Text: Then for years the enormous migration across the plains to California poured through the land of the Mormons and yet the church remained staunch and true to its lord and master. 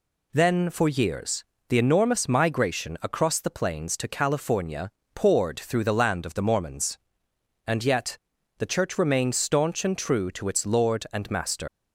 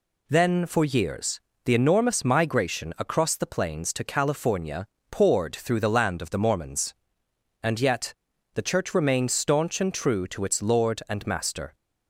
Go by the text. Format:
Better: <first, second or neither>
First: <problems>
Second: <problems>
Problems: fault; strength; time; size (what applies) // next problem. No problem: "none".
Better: second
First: pauses between "years" and "the"; slight; at 1.4 s; 0.26 s long // pauses between "California" and "poured"; slight; at 4.8 s; 0.24 s long // pauses between "yet" and "the"; at 8.1 s; 0.40 s long // leaves "master" unfinished; at 11.6 s; 100 ms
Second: pauses between "years" and "the"; slight; at 1.3 s; 0.26 s long // pauses between "California" and "poured"; slight; at 4.8 s; 0.24 s long // pauses between "yet" and "the"; at 8.1 s; 0.40 s long